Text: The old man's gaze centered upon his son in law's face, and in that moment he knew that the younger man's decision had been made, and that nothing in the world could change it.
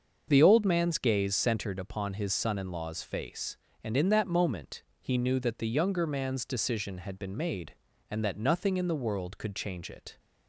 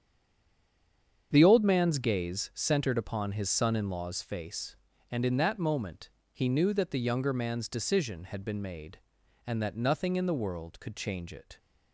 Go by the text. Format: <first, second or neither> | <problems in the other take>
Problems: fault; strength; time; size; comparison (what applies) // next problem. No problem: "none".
first | stays silent before the first word; noticeable; until 1.3 s; 1.3 s long // starts louder than the rest; strong; until 2.3 s; 7.5 dB; also in the first // pauses between "moment" and "he"; slight; at 6.0 s; 0.20 s long; slight in the first